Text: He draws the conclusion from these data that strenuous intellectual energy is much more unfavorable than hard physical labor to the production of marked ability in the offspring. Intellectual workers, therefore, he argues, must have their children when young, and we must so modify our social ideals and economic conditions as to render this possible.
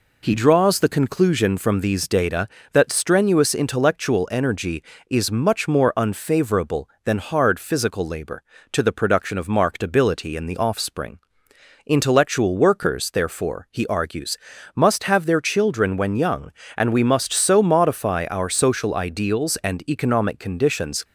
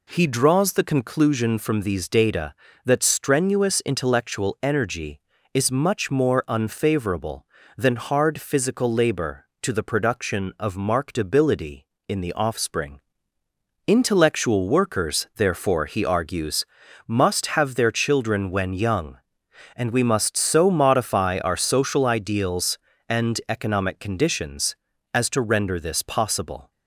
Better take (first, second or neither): second